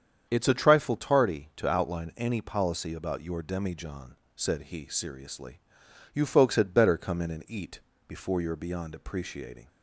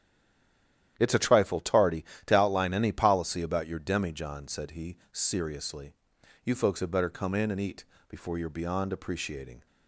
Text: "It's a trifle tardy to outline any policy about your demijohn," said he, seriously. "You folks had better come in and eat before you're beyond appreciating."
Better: first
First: starts louder than the rest; strong; until 1.3 s; 8 dB // pauses between "eat" and "before"; slight; at 7.7 s; 0.28 s long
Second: stays silent before the first word; until 0.9 s; 0.9 s long // starts louder than the rest; strong; until 1.9 s; 10.5 dB // pauses between "eat" and "before"; slight; at 7.8 s; 0.24 s long

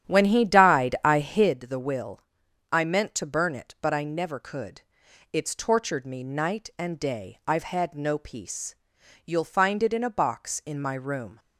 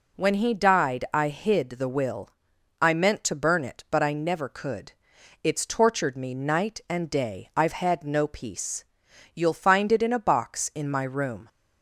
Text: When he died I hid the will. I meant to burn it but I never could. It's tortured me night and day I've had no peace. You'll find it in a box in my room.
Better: second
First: starts louder than the rest; strong; until 1.6 s; 10 dB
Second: none

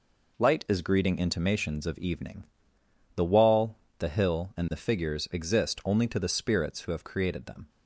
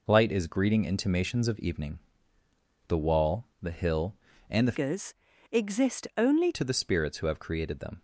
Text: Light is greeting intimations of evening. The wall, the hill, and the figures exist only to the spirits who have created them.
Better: first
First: none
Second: changes voice from "figures" to "only"; from 4.7 to 6.5 s; 1.8 s long // pauses between "figures" and "exist"; slight; at 5.1 s; 0.36 s long

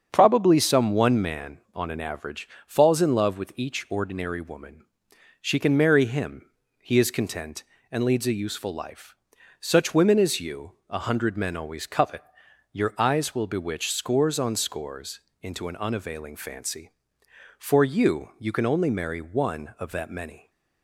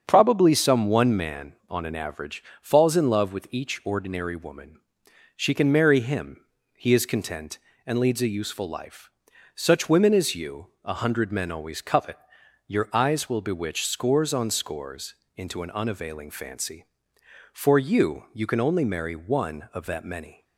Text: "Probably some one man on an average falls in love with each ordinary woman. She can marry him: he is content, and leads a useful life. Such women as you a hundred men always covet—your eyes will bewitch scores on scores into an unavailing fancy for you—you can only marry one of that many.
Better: neither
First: starts louder than the rest; strong; until 1.1 s; 7.5 dB // pauses between "average" and "falls"; slight; at 2.4 s; 0.18 s long // pauses between "you" and "a"; slight; at 10.7 s; 0.16 s long // pauses between "scores" and "into"; slight; at 15.1 s; 0.22 s long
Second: starts louder than the rest; strong; until 1.0 s; 7.5 dB // pauses between "average" and "falls"; slight; at 2.4 s; 0.18 s long // pauses between "you" and "a"; slight; at 10.6 s; 0.16 s long // pauses between "scores" and "into"; slight; at 15.1 s; 0.22 s long

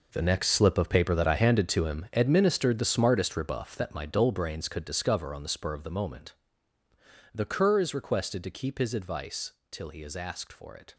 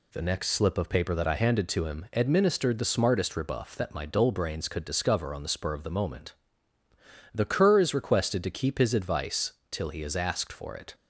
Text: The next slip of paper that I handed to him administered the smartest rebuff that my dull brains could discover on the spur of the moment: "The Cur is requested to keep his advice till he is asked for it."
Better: second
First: gets quieter; strong; throughout; 13.5 dB // pauses between "advice" and "till"; slight; at 9.5 s; 0.18 s long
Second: pauses between "advice" and "till"; slight; at 9.5 s; 0.18 s long

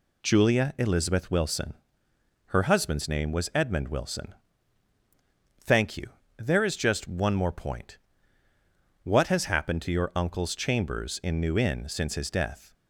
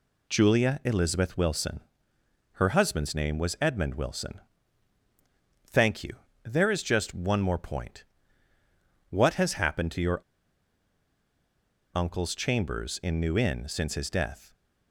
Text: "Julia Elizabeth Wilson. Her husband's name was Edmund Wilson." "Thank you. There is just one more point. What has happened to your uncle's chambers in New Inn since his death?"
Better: first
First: none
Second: pauses between "your" and "uncle's"; strong; at 10.2 s; 1.7 s long

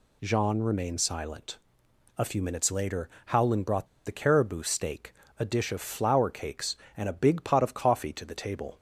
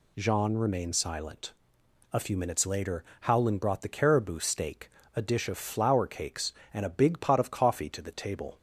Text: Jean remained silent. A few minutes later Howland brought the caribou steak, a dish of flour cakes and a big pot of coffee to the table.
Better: second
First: pauses between "later" and "Howland"; slight; at 3.0 s; 0.20 s long // pauses between "brought" and "the"; slight; at 3.8 s; 0.20 s long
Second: pauses between "later" and "Howland"; slight; at 3.0 s; 0.20 s long

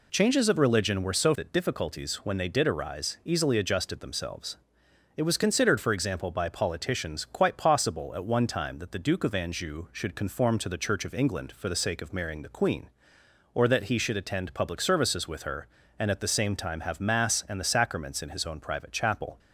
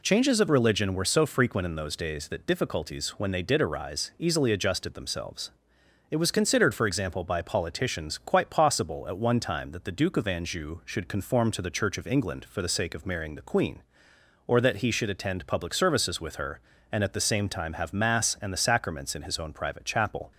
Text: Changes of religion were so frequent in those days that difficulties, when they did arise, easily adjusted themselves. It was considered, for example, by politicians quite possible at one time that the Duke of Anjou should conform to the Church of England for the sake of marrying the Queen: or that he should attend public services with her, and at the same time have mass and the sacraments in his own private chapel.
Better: second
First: skips "frequent in those days"; at 1.3 s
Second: none

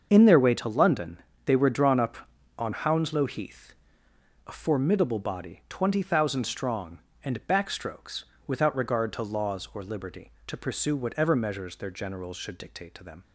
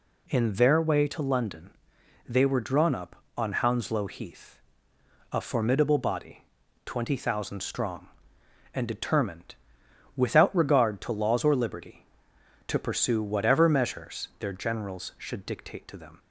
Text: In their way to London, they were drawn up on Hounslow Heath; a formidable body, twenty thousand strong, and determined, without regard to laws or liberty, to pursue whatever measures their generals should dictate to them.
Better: second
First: starts louder than the rest; until 1.1 s; 6.5 dB // says "backstrokes" for "determined"; at 7.4 s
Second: none

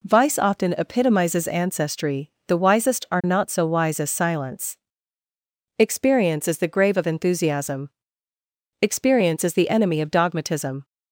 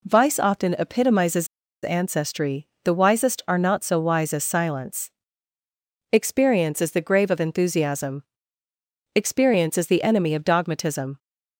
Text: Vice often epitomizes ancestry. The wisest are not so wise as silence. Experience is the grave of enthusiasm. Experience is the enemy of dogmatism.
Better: first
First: none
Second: pauses between "epitomizes" and "ancestry"; at 1.4 s; 0.36 s long

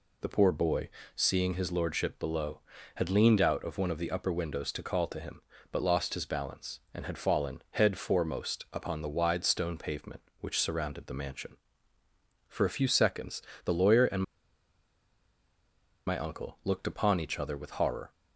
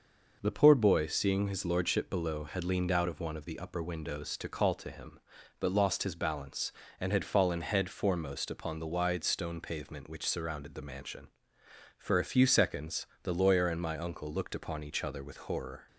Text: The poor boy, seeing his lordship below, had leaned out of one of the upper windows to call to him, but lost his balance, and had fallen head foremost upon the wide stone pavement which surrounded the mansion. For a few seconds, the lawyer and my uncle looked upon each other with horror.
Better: second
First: pauses between "and" and "my"; strong; at 14.2 s; 1.8 s long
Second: none

